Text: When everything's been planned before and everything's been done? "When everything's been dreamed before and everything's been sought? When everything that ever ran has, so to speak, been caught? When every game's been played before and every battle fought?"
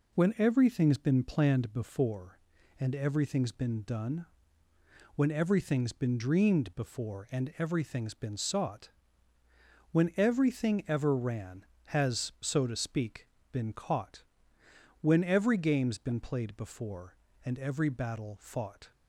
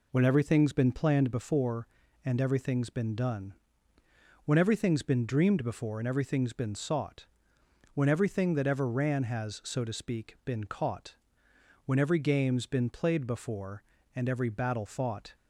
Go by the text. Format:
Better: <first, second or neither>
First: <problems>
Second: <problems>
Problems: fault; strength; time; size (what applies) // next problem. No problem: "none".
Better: second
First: skips "that"; at 10.8 s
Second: none